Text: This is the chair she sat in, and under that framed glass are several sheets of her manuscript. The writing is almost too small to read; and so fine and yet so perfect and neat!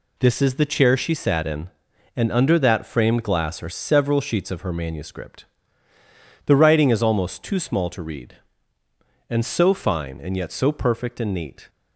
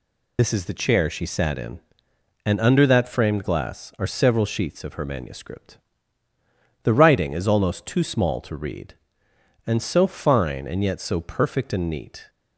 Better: first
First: none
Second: loses the start of "This"; at 0.3 s; 80 ms

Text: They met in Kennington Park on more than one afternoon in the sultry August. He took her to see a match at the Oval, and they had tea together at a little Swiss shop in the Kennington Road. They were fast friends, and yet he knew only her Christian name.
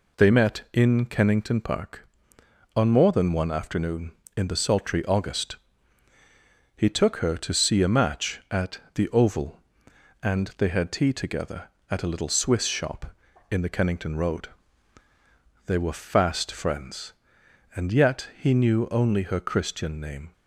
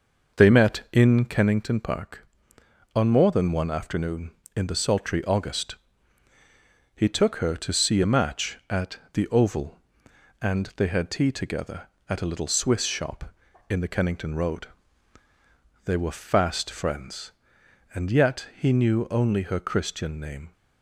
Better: first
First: none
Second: starts louder than the rest; noticeable; until 1.4 s; 6 dB

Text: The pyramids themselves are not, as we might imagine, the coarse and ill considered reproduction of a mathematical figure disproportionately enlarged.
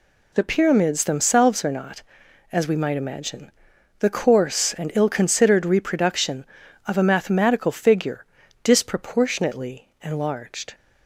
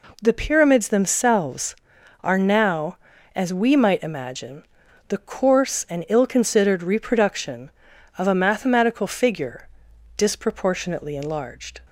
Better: first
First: pauses between "figure" and "disproportionately"; at 8.2 s; 0.38 s long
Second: says "now" for "not"; at 2.3 s // pauses between "figure" and "disproportionately"; noticeable; at 9.6 s; 0.50 s long

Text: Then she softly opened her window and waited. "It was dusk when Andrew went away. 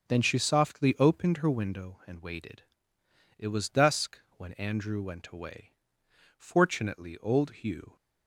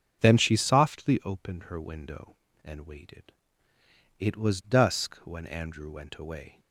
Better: second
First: starts louder than the rest; until 1.1 s; 7 dB // pauses between "dusk" and "when"; slight; at 4.1 s; 0.18 s long // goes on to say "Fortunately old Hugh"; from 6.3 s on; 1.6 s long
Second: starts louder than the rest; until 1.2 s; 7 dB

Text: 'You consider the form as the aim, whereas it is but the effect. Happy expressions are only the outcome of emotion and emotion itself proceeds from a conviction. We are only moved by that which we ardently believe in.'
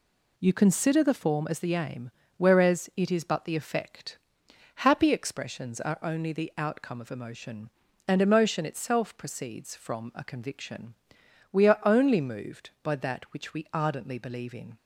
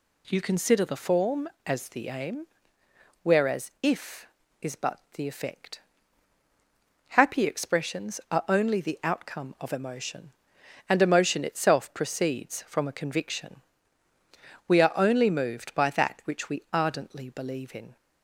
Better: first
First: none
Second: says "if" for "it"; at 3.8 s

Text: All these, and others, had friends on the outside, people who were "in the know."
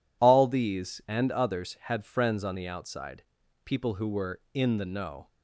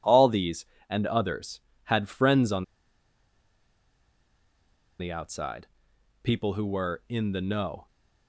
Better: first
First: none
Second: pauses between "on" and "the"; strong; at 2.6 s; 2.3 s long

